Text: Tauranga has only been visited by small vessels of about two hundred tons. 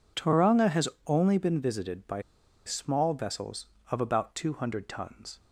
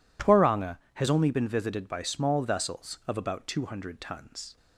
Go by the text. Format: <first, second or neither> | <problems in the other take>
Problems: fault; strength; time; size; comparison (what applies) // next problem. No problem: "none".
second | pauses between "has" and "only"; slight; at 0.8 s; 0.20 s long // pauses between "by" and "small"; at 2.2 s; 0.43 s long